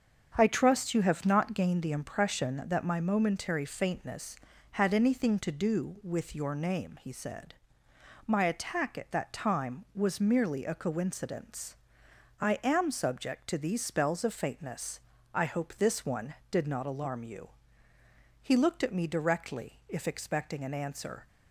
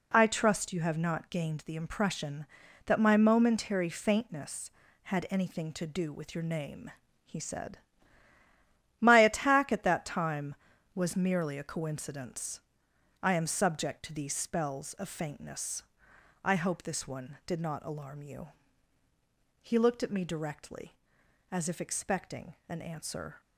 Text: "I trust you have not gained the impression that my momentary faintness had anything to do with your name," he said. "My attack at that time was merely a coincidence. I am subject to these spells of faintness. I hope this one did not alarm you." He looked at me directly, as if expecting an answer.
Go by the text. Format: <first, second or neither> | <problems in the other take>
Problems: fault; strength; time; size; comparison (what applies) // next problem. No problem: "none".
second | starts louder than the rest; until 1.3 s; 7 dB // skips "as"; at 19.8 s